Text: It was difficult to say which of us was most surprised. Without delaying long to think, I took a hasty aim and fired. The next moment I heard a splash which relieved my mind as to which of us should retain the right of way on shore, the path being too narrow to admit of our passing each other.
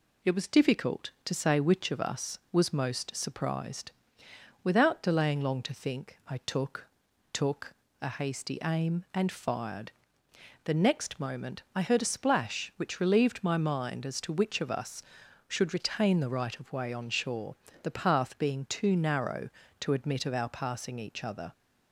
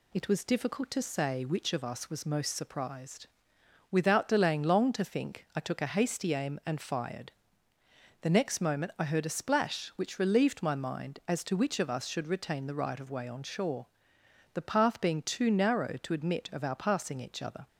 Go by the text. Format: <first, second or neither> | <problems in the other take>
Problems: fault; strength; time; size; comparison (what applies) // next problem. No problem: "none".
second | says "took" twice; at 7.3 s